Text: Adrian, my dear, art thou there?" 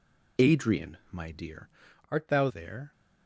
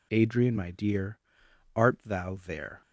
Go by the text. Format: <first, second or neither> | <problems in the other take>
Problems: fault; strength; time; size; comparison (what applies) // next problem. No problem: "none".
second | changes voice from "art" to "thou"; from 2.0 to 2.4 s; 0.4 s long